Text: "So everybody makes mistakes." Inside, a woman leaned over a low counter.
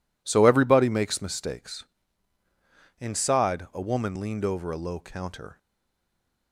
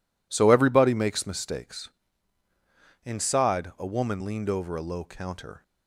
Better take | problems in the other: second | stays silent after the last word; slight; from 5.5 s on; 1.0 s long

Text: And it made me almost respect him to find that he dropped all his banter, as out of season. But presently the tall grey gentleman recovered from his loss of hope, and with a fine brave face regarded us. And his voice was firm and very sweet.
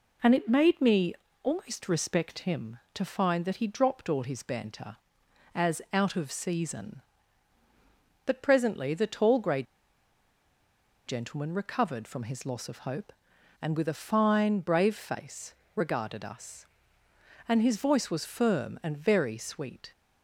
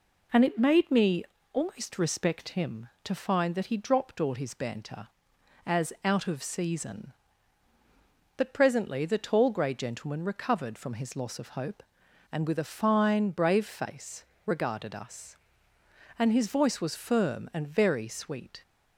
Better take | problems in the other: second | pauses between "me" and "almost"; slight; at 1.1 s; 0.28 s long; slight in the second // pauses between "grey" and "gentleman"; strong; at 9.6 s; 1.4 s long // pauses between "face" and "regarded"; slight; at 15.5 s; 0.22 s long; slight in the second

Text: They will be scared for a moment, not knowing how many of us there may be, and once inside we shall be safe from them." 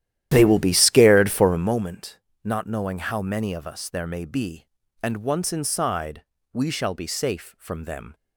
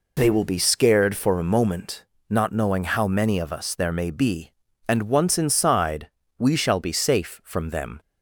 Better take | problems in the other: second | starts louder than the rest; strong; until 1.8 s; 12 dB // pauses between "inside" and "we"; slight; at 6.2 s; 0.32 s long; slight in the second

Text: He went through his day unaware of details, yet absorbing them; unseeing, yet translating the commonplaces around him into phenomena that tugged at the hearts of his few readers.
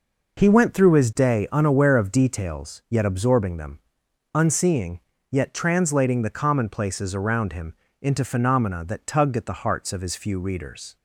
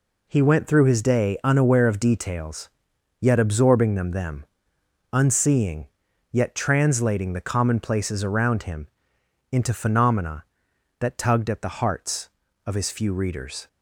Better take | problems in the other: first | says "them" twice; at 4.0 s // pauses between "him" and "into"; noticeable; at 8.8 s; 0.64 s long; slight in the first

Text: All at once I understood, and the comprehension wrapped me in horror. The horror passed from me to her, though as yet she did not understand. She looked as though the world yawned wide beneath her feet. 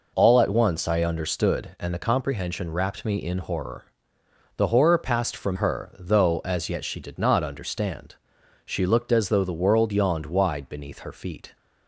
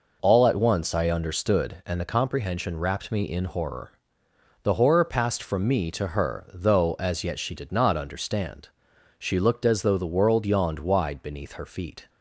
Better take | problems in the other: second | skips "me to"; at 5.5 s

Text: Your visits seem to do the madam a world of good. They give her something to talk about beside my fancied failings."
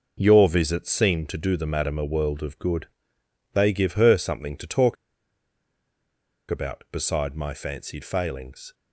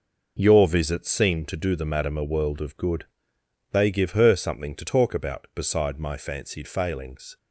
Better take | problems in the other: second | pauses between "talk" and "about"; strong; at 4.9 s; 1.5 s long

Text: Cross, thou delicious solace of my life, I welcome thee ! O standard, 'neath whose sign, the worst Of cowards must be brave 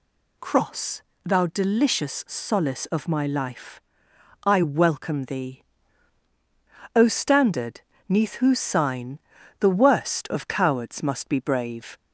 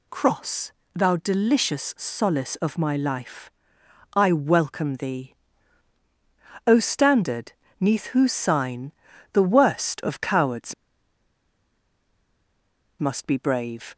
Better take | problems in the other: first | pauses between "cowards" and "must"; strong; at 10.7 s; 2.2 s long

